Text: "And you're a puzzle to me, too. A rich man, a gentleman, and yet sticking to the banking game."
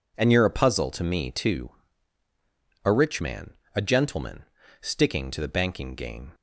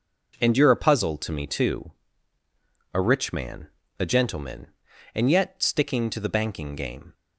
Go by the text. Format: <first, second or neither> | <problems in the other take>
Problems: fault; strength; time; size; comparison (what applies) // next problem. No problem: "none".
second | skips "and yet"; at 4.6 s